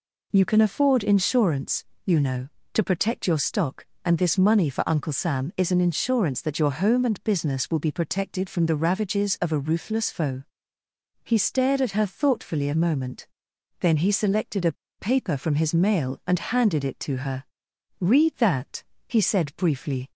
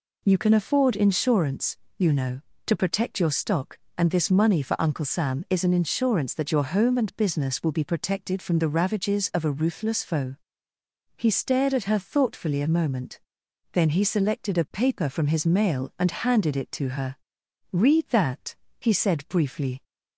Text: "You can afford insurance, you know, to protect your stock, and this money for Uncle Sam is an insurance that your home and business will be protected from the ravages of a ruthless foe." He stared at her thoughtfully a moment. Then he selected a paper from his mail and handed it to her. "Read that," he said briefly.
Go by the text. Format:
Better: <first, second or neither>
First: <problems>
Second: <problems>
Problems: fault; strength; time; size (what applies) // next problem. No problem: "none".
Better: second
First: pauses between "a" and "paper"; slight; at 14.7 s; 0.25 s long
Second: none